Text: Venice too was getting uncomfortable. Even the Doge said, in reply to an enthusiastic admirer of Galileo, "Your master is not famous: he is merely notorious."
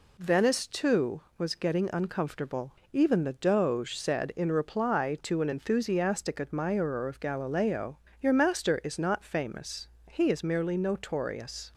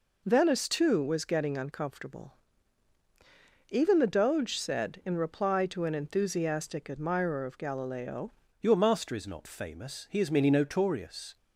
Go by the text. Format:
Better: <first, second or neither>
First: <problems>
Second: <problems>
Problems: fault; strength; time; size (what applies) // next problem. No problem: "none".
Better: first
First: none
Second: changes voice at "Your"; from 8.5 s on; 2.8 s long